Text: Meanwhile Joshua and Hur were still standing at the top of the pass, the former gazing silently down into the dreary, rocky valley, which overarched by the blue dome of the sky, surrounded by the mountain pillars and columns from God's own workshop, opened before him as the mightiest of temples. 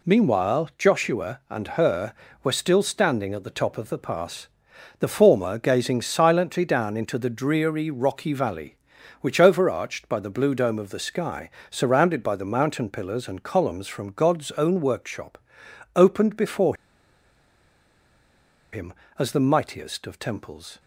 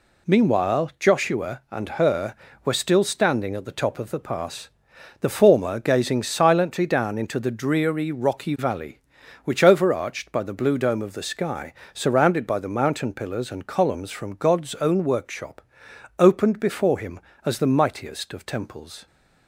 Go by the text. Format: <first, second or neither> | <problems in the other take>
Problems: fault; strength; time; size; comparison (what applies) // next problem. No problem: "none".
second | pauses between "before" and "him"; strong; at 16.7 s; 1.9 s long